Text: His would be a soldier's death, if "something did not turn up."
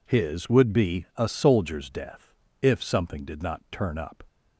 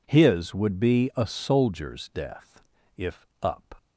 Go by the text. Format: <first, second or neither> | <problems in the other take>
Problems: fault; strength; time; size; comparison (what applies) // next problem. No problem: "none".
first | skips "something did not turn"; at 3.3 s